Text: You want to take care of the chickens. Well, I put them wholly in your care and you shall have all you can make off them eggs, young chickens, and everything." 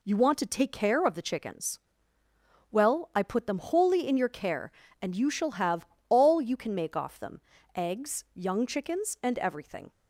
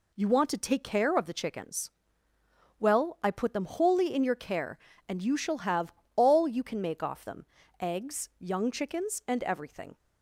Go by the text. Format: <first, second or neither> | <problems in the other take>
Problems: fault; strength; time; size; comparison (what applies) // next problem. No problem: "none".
neither | pauses between "have" and "all"; slight; the same in both // pauses between "them" and "eggs"; slight; the same in both